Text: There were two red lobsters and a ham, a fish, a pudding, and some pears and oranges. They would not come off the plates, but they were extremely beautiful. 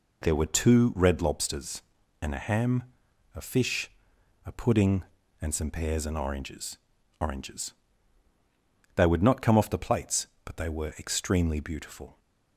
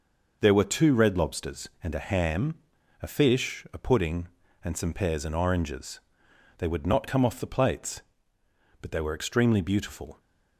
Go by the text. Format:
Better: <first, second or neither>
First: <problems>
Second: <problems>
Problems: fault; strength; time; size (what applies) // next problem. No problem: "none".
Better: second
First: says "oranges" twice; at 7.1 s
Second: none